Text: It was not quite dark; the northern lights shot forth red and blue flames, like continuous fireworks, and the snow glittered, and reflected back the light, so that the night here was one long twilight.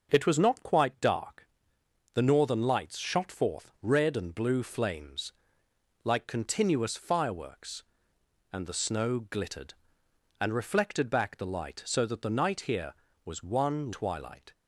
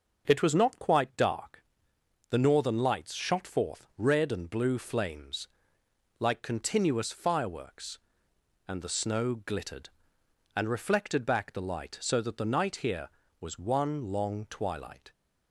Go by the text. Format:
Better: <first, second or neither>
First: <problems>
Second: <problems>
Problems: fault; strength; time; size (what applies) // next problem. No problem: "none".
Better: second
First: starts louder than the rest; noticeable; until 1.1 s; 6 dB // skips "long"; at 13.9 s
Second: starts louder than the rest; noticeable; until 1.2 s; 6 dB